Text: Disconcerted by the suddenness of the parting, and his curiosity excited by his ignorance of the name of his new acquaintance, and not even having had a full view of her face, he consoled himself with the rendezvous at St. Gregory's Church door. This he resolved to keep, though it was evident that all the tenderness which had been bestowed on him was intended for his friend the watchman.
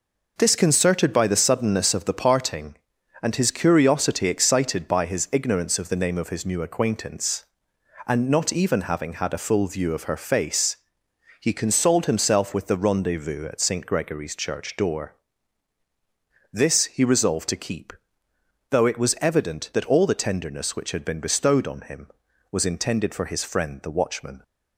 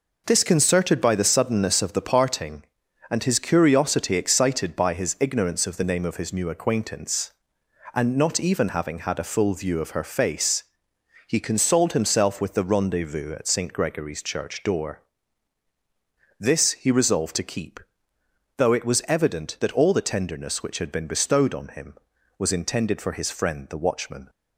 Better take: neither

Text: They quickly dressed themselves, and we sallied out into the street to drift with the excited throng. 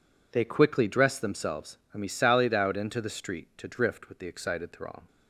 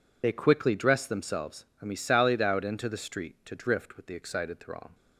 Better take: first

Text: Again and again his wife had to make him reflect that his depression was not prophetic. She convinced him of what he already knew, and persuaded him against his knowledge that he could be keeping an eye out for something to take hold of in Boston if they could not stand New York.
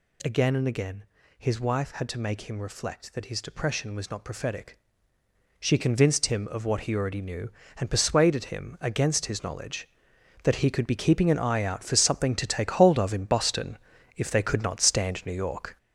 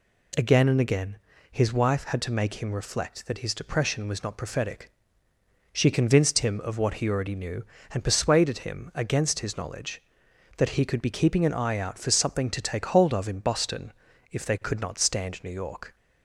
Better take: second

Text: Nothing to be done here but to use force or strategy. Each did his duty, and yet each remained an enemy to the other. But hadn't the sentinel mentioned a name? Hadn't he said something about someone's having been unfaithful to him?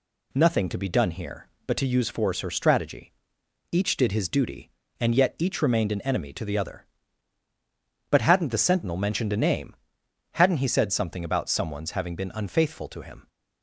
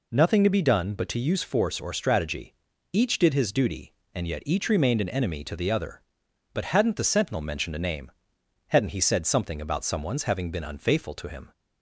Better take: first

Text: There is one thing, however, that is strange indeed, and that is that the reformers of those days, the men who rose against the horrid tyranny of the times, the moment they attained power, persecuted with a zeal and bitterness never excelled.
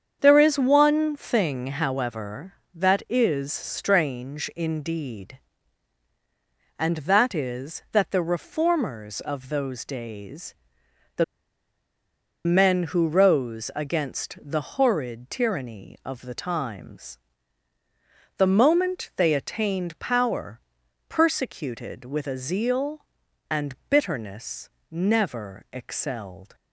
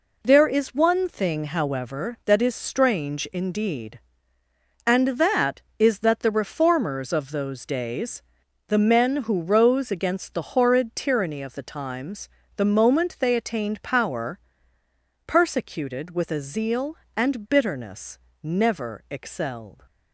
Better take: second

